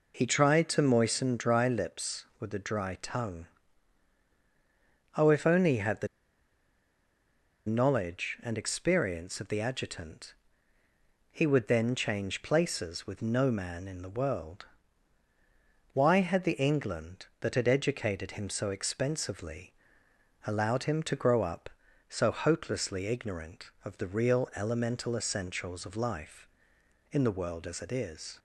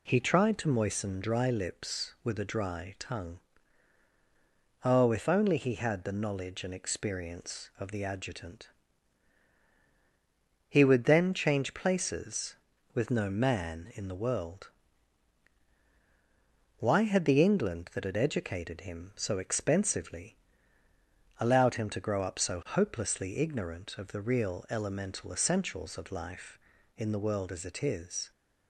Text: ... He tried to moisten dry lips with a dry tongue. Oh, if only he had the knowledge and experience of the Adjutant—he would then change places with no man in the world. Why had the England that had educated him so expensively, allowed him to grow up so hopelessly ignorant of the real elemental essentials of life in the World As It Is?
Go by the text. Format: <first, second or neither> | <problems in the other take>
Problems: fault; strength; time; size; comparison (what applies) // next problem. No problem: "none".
second | pauses between "the" and "knowledge"; strong; at 6.0 s; 1.5 s long